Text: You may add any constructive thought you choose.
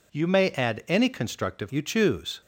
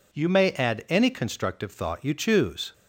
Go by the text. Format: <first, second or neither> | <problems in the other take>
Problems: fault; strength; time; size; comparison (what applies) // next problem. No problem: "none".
second | skips "thought"; at 1.6 s